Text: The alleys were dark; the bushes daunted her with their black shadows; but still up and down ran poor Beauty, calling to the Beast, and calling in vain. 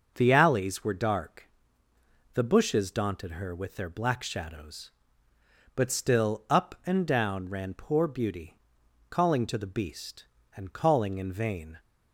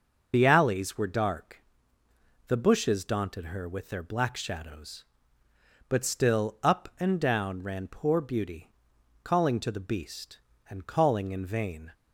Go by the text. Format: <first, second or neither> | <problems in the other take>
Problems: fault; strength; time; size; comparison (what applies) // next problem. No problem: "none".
first | loses the start of "The"; at 0.3 s; 50 ms // starts louder than the rest; until 1.3 s; 6.5 dB; also in the first